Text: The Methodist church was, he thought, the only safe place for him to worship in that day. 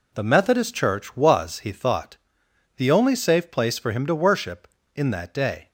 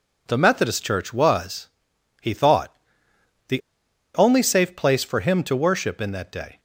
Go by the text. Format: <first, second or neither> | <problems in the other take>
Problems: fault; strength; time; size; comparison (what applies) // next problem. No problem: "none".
first | pauses between "the" and "only"; noticeable; at 3.6 s; 0.54 s long